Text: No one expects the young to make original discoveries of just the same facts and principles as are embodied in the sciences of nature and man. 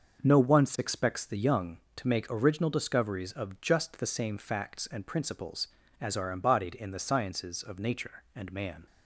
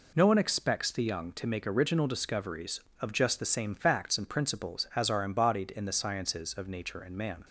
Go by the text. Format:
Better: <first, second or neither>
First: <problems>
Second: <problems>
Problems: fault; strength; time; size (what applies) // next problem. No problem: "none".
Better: second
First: starts louder than the rest; until 1.2 s; 6 dB // says "once" for "one"; at 0.3 s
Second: none